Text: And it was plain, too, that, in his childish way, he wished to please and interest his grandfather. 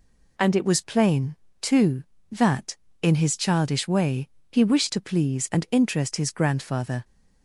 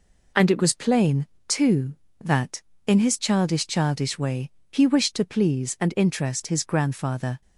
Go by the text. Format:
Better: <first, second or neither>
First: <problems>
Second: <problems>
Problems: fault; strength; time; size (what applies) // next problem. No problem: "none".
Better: first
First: none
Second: says "childish" twice; at 3.6 s